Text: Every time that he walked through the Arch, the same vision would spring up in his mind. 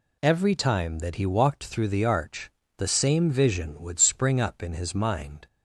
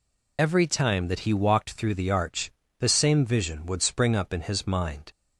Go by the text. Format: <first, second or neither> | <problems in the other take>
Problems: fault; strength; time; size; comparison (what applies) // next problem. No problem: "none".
first | loses the start of "Every"; at 0.3 s; 45 ms